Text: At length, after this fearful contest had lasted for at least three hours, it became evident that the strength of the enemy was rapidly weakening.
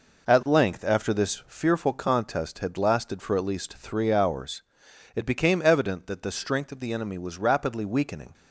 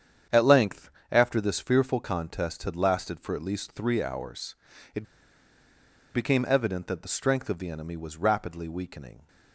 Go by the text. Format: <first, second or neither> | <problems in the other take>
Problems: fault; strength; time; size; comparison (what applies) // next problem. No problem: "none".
first | starts louder than the rest; strong; until 1.5 s; 8.5 dB // pauses between "it" and "became"; at 5.0 s; 1.1 s long